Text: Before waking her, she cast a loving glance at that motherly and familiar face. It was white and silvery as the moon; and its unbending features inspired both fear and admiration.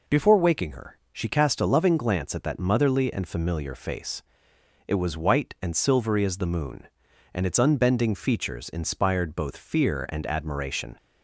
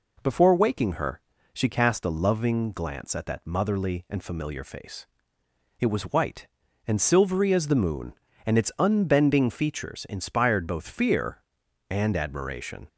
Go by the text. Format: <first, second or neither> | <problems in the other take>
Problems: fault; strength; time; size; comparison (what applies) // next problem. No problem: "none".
neither | none